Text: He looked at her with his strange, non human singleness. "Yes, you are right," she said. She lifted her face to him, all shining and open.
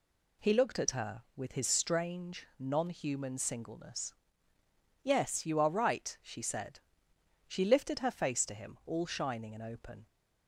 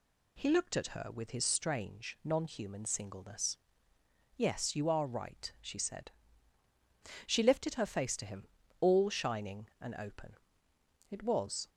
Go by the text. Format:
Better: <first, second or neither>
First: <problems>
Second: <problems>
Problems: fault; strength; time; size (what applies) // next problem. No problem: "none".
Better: first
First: none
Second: goes on to say "It was"; from 11.0 s on; 0.60 s long